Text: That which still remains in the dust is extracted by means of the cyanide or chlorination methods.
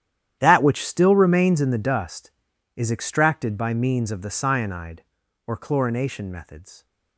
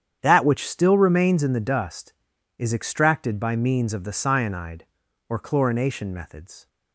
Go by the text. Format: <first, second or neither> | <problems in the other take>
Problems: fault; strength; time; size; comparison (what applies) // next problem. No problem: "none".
second | gets quieter; strong; throughout; 17.5 dB // starts louder than the rest; strong; until 1.4 s; 10.5 dB; strong in the second